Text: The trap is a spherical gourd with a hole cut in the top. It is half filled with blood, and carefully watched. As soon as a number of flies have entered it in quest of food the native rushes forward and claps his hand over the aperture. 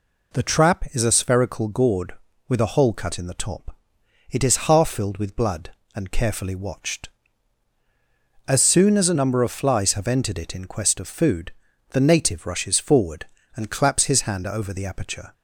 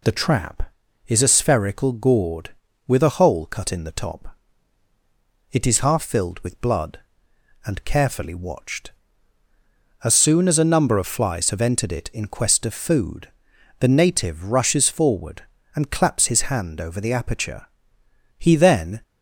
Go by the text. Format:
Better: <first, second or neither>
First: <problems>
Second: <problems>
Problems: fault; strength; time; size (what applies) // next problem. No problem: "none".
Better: first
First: pauses between "food" and "the"; at 11.5 s; 0.38 s long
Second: pauses between "food" and "the"; noticeable; at 13.2 s; 0.50 s long // goes on to say "He then"; noticeable; from 18.3 s on; 0.64 s long